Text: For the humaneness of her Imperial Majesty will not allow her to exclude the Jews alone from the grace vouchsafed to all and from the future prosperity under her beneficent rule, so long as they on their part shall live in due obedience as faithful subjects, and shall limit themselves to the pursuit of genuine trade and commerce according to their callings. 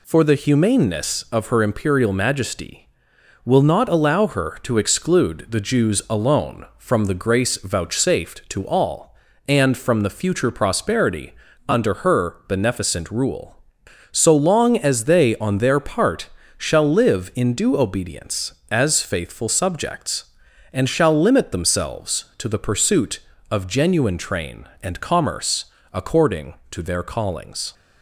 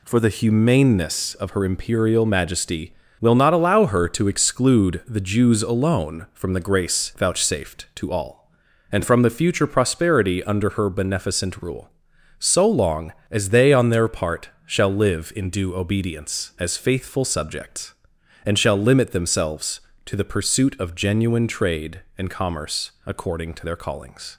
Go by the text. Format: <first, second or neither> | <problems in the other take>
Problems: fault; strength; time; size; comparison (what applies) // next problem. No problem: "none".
second | pauses between "prosperity" and "under"; slight; at 11.3 s; 0.34 s long // pauses between "part" and "shall"; slight; at 16.2 s; 0.26 s long; slight in the second // says "train" for "trade"; at 24.1 s // pauses between "commerce" and "according"; slight; at 25.6 s; 0.26 s long